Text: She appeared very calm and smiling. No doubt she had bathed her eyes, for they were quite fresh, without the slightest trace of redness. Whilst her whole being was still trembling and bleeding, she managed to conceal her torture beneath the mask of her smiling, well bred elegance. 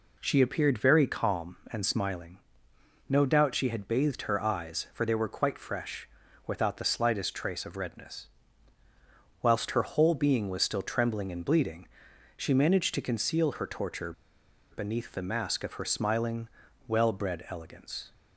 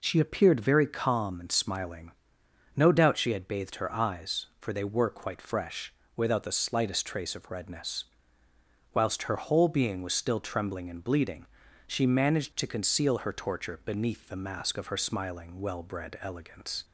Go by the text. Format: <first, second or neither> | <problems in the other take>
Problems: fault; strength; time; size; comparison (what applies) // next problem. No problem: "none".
second | pauses between "torture" and "beneath"; noticeable; at 14.1 s; 0.59 s long